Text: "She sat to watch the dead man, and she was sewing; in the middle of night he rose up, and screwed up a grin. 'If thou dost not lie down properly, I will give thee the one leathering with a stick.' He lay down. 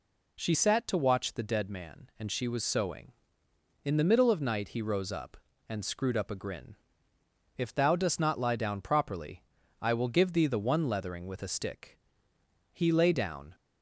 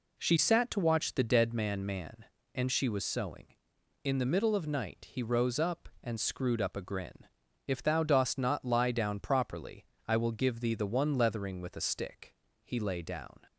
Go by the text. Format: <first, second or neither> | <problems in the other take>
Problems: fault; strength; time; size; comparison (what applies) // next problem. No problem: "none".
first | says "man" twice; at 1.8 s